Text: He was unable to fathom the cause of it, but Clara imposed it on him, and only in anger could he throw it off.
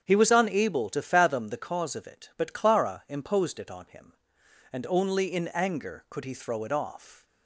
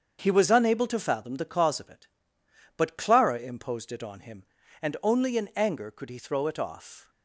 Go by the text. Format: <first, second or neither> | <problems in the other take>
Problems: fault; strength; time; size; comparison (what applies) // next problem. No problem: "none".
neither | starts louder than the rest; the same in both